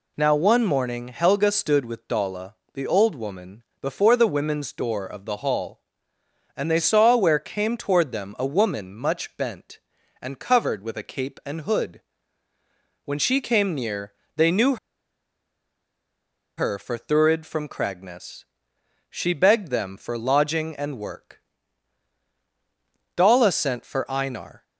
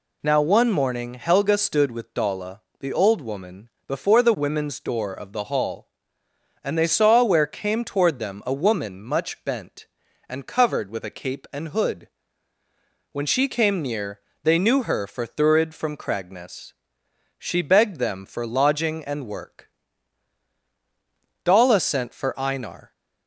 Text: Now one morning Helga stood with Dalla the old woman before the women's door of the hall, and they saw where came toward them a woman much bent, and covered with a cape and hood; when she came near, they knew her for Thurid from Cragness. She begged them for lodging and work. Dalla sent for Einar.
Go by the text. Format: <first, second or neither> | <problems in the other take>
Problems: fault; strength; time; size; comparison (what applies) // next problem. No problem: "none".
second | pauses between "Dalla" and "the"; slight; at 2.5 s; 0.20 s long; slight in the second // pauses between "woman" and "before"; slight; at 3.6 s; 0.18 s long; slight in the second // pauses between "knew" and "her"; strong; at 14.7 s; 1.8 s long